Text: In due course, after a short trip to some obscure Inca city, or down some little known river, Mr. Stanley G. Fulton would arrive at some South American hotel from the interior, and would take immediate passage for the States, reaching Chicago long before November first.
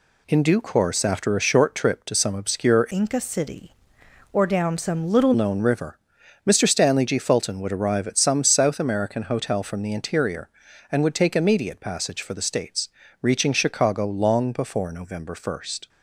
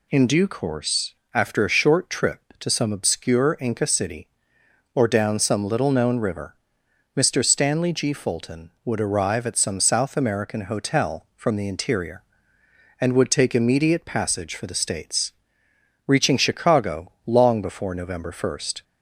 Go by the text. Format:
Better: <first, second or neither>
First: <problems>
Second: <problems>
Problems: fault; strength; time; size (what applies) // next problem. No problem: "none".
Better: second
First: changes voice from "Inca" to "little"; from 2.9 to 5.3 s; 2.4 s long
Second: none